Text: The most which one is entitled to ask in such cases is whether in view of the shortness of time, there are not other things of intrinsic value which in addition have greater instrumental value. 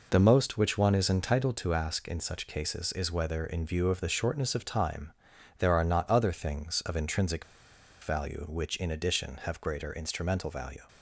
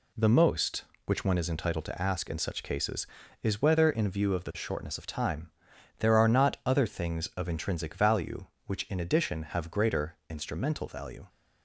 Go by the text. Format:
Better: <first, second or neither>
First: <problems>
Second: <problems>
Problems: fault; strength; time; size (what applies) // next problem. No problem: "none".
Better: second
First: pauses between "intrinsic" and "value"; noticeable; at 7.4 s; 0.60 s long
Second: none